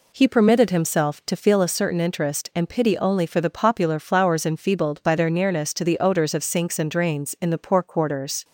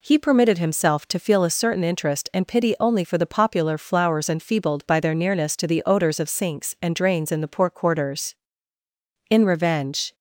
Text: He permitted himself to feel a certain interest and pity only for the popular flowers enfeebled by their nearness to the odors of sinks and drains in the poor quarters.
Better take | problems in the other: first | goes on to say "In revenge"; noticeable; from 9.2 s on; 0.86 s long

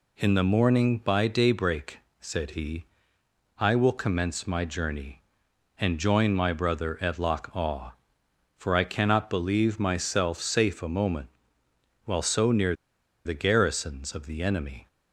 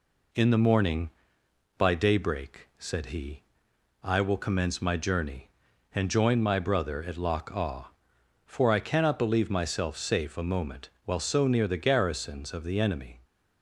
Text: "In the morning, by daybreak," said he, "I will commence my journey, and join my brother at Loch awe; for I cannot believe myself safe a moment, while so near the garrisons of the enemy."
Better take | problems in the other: second | pauses between "near" and "the"; noticeable; at 12.7 s; 0.51 s long

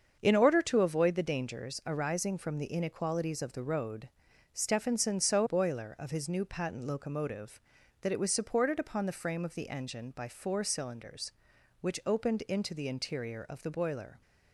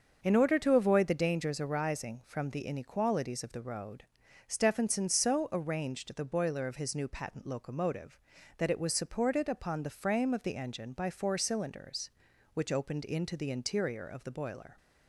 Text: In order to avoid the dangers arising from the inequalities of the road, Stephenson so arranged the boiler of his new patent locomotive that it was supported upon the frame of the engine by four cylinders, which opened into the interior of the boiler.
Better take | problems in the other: second | starts louder than the rest; until 1.2 s; 7 dB; also in the second // skips "arranged the"; at 5.4 s

